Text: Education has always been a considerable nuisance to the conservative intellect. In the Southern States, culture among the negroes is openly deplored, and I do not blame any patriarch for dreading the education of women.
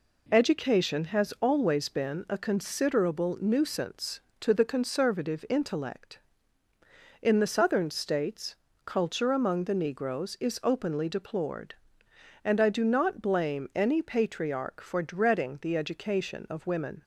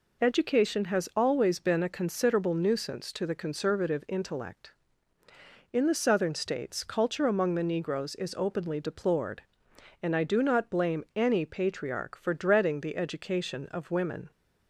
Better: neither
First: none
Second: none

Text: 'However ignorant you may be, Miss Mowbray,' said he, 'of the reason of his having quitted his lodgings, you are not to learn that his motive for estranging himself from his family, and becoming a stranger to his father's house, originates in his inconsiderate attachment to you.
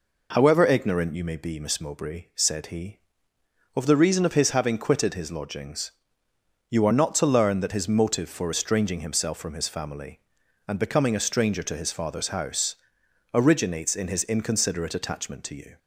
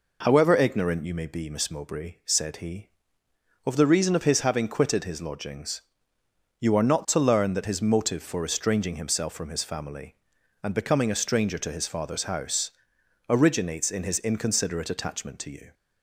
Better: neither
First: none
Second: none

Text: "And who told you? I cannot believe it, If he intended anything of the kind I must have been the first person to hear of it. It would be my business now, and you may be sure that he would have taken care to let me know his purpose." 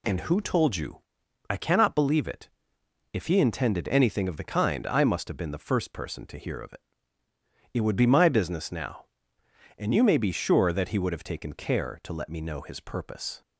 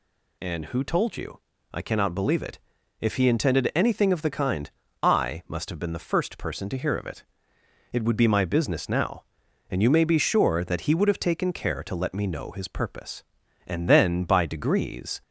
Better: first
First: none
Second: pauses between "kind" and "I"; slight; at 4.6 s; 0.32 s long // goes on to say "And then by degrees"; from 13.6 s on; 1.5 s long

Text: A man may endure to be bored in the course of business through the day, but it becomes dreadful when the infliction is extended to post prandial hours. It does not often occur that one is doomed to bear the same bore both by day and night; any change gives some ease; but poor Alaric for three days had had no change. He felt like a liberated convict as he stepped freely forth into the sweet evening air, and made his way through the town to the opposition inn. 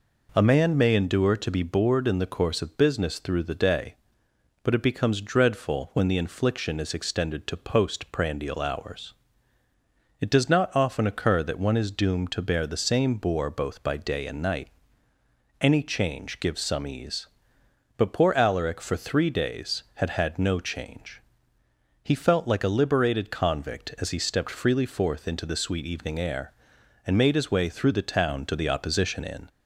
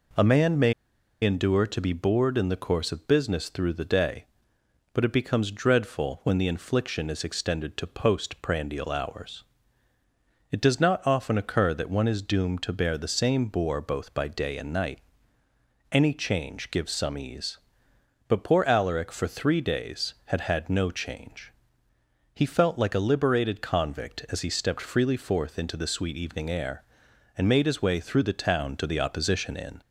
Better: first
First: none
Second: pauses between "may" and "endure"; noticeable; at 0.7 s; 0.51 s long

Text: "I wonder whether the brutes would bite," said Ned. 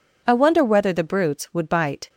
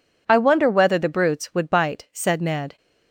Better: second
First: stops before "said Ned"; at 2.0 s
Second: none

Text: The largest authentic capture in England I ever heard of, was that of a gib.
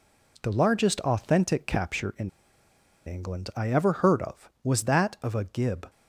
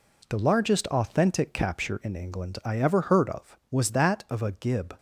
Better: second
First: pauses between "in" and "England"; noticeable; at 2.2 s; 0.77 s long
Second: none

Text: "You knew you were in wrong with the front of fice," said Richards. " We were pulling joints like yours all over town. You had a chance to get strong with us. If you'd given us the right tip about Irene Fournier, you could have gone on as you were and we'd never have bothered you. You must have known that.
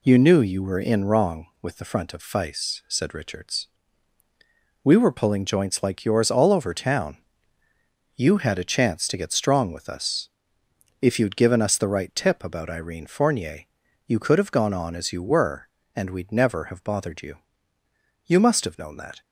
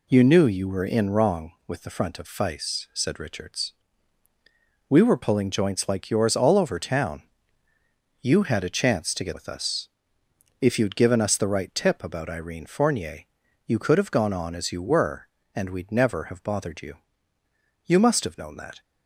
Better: first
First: none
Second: skips "strong"; at 9.3 s

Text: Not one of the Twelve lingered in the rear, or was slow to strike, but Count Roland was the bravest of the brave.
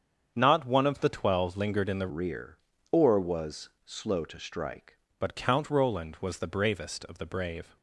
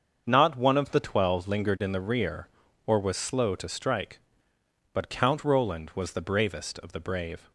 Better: second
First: starts louder than the rest; strong; until 1.3 s; 7.5 dB // changes voice from "rear" to "strike"; from 2.0 to 4.9 s; 2.9 s long // pauses between "was" and "slow"; slight; at 3.6 s; 0.16 s long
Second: starts louder than the rest; until 1.2 s; 7 dB

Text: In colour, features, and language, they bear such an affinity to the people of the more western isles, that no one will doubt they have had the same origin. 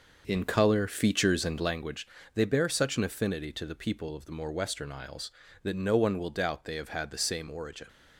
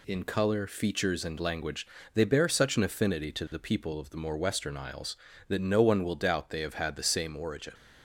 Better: second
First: starts louder than the rest; noticeable; until 1.9 s; 6 dB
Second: none

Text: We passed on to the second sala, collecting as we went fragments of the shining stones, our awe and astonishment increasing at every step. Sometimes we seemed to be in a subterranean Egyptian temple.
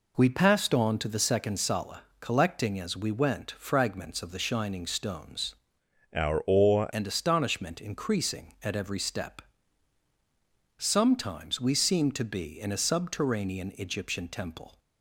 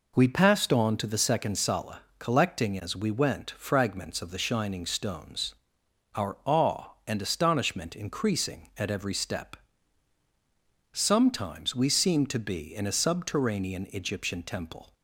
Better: second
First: changes voice from "our" to "awe"; from 6.1 to 6.8 s; 0.7 s long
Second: none

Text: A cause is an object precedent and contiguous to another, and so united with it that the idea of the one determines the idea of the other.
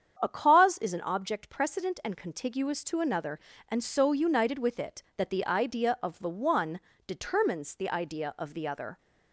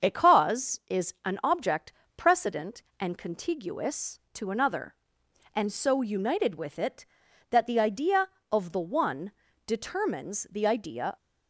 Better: first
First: starts louder than the rest; strong; until 1.2 s; 8 dB // pauses between "one" and "determines"; slight; at 6.7 s; 0.26 s long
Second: starts louder than the rest; until 1.1 s; 7 dB // pauses between "object" and "precedent"; slight; at 1.9 s; 0.24 s long // pauses between "one" and "determines"; slight; at 9.3 s; 0.36 s long // stops before "of the other"; at 11.1 s

